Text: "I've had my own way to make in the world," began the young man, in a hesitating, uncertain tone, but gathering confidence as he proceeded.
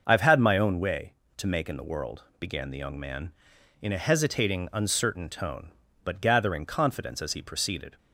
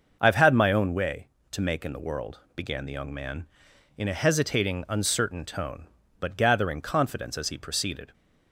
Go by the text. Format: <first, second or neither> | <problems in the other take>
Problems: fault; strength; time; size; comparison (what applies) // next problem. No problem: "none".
neither | starts louder than the rest; noticeable; the same in both